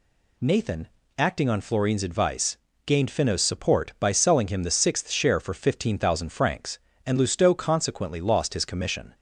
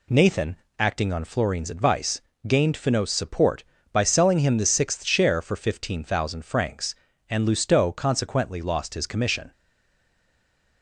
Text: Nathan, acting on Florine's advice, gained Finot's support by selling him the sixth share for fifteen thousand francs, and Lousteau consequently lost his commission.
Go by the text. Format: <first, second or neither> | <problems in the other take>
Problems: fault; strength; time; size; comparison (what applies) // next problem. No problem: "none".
first | stays silent after the last word; noticeable; from 9.5 s on; 1.3 s long